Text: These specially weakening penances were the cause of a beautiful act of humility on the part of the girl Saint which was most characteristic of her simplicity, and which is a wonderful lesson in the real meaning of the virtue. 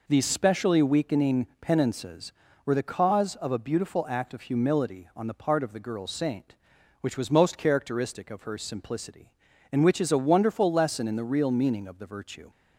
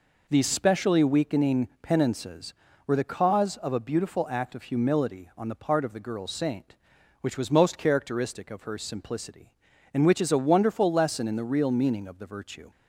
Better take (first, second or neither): neither